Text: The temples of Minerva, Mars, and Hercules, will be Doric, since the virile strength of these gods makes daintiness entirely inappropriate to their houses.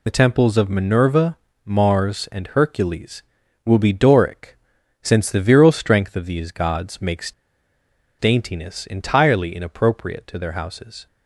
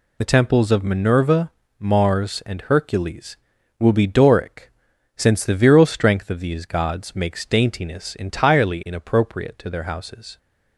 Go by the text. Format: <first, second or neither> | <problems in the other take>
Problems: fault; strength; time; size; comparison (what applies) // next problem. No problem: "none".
second | pauses between "makes" and "daintiness"; noticeable; at 7.3 s; 0.87 s long